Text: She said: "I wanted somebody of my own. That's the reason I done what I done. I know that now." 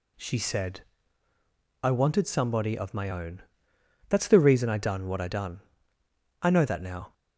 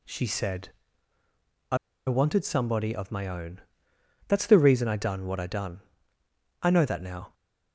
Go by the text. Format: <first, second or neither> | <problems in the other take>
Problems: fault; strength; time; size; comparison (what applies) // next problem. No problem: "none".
first | pauses between "I" and "wanted"; slight; at 1.7 s; 0.29 s long